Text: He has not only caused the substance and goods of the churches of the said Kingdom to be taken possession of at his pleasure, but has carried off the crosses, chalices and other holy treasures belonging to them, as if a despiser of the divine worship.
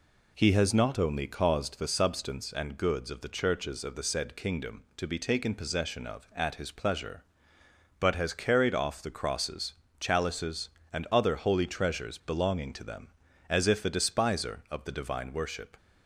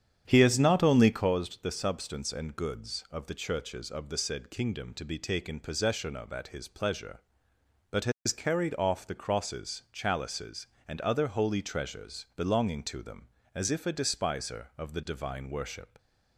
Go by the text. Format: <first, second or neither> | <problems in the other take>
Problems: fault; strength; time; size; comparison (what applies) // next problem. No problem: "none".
first | starts louder than the rest; strong; until 1.3 s; 9 dB